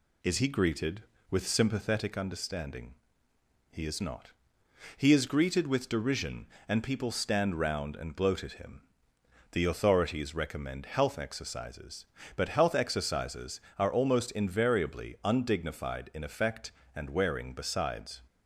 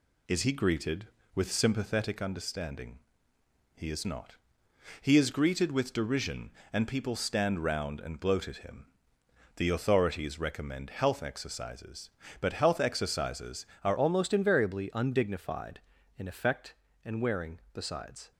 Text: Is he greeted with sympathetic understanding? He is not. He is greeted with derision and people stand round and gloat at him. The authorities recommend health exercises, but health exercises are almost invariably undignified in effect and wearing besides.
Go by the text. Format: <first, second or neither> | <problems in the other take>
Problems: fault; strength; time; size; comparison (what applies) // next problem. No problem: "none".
first | changes voice at "almost"; from 13.9 s on; 4.4 s long